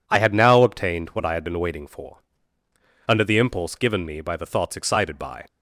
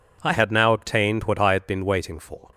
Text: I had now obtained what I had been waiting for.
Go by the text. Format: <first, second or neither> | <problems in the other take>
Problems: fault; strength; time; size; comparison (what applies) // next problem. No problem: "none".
second | goes on to say "Under the impulse given me by the thoughts excited by"; strong; from 3.0 s on; 2.3 s long